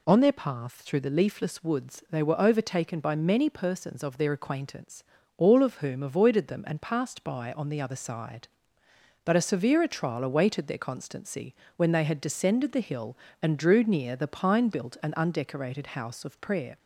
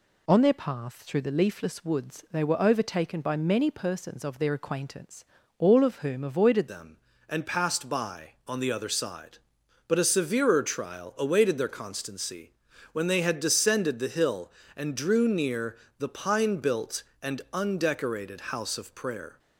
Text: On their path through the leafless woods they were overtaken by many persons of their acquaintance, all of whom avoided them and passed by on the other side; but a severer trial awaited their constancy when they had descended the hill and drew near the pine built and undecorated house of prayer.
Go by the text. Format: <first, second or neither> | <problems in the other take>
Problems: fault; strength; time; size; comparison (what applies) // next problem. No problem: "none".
first | changes voice at "them"; from 6.6 s on; 12.7 s long // pauses between "constancy" and "when"; at 12.5 s; 0.40 s long; slight in the first // pauses between "near" and "the"; slight; at 15.7 s; 0.22 s long